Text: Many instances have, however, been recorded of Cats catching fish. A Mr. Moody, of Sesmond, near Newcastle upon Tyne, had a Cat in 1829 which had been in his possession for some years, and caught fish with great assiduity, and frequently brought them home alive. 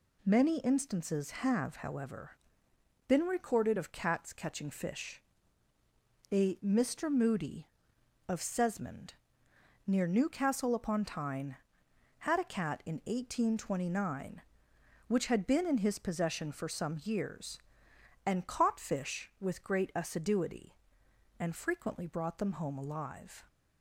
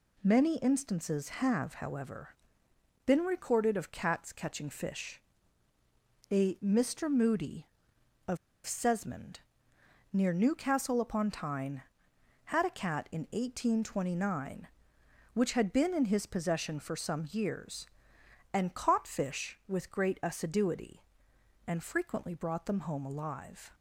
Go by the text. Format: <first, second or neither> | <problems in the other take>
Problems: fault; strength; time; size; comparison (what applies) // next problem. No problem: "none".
first | pauses between "of" and "Sesmond"; slight; at 8.3 s; 0.29 s long